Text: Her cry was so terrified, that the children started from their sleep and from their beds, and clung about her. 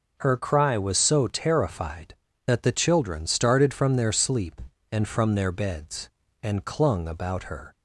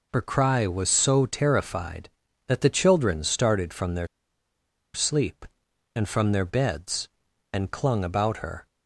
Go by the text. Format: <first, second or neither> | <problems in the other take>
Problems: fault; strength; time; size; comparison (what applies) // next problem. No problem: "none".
first | pauses between "their" and "sleep"; noticeable; at 4.0 s; 0.87 s long